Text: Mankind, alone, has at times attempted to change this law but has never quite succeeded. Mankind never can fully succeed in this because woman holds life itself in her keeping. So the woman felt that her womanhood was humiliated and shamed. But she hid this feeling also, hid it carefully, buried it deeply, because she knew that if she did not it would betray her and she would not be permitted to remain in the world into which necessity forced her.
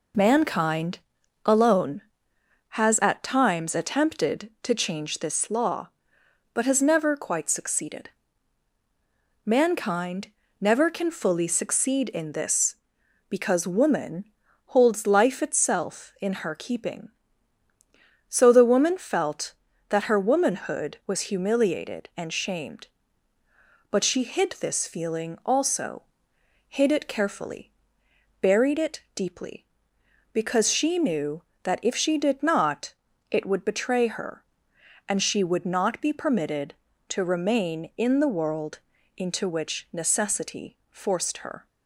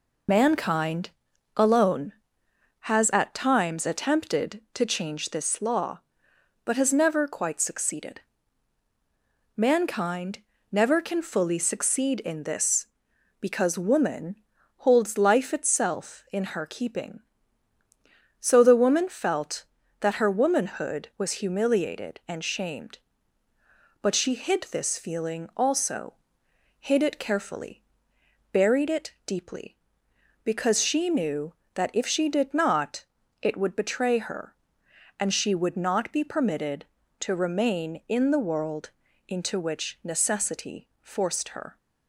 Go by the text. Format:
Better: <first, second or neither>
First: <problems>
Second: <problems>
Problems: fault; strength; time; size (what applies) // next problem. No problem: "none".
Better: first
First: pauses between "Mankind" and "never"; slight; at 10.2 s; 0.30 s long // pauses between "woman" and "holds"; at 14.2 s; 0.44 s long // pauses between "not" and "it"; at 32.9 s; 0.40 s long // pauses between "world" and "into"; slight; at 38.7 s; 0.36 s long // pauses between "necessity" and "forced"; slight; at 40.7 s; 0.16 s long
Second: loses the start of "Mankind"; at 0.2 s; 30 ms // pauses between "Mankind" and "never"; slight; at 10.3 s; 0.30 s long // pauses between "woman" and "holds"; at 14.3 s; 0.44 s long // pauses between "not" and "it"; at 33.0 s; 0.40 s long // pauses between "world" and "into"; slight; at 38.9 s; 0.36 s long // pauses between "necessity" and "forced"; slight; at 40.8 s; 0.16 s long